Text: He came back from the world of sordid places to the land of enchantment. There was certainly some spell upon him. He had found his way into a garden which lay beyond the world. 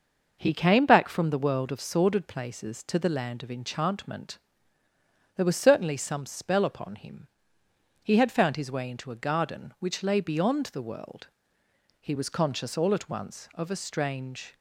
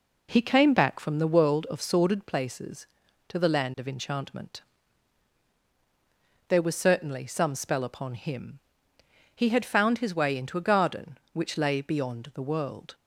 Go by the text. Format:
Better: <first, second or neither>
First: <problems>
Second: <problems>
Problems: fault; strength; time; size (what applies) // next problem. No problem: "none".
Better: second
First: goes on to say "He was conscious all at once of a strange"; strong; from 11.9 s on; 2.5 s long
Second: none